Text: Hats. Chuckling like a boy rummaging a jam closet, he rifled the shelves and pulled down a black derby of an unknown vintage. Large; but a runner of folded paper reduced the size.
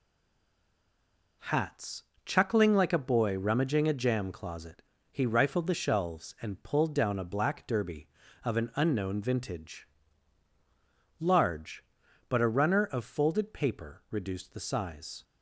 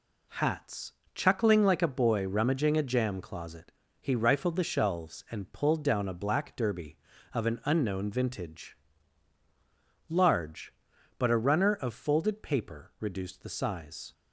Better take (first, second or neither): second